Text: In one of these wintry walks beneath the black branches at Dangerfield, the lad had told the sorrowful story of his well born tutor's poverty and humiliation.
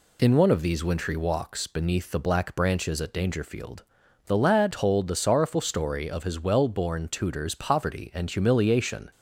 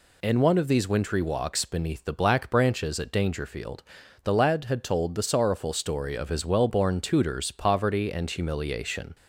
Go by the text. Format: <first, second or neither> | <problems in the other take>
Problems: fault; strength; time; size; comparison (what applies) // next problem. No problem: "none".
second | skips "had"; at 4.7 s